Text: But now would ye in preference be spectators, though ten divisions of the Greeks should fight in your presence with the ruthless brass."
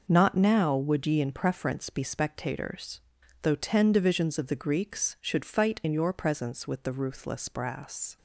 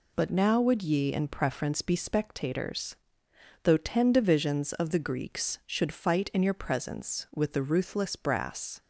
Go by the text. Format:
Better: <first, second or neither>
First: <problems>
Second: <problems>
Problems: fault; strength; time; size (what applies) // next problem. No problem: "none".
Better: second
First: says "Not" for "But"; at 0.0 s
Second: none